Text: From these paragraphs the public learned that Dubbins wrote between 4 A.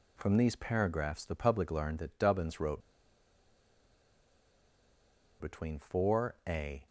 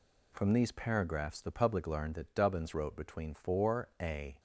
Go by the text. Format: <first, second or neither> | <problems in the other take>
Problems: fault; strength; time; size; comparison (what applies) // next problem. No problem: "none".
second | pauses between "wrote" and "between"; strong; at 2.8 s; 2.5 s long